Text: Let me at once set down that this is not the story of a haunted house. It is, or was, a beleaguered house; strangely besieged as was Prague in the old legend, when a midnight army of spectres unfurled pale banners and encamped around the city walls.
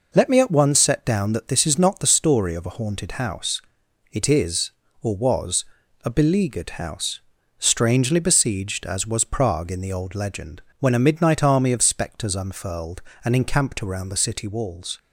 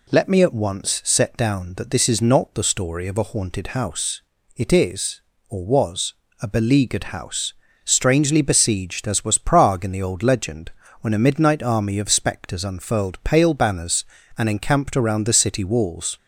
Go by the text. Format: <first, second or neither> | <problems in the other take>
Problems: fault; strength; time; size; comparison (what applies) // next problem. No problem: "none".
second | skips "pale banners"; at 13.1 s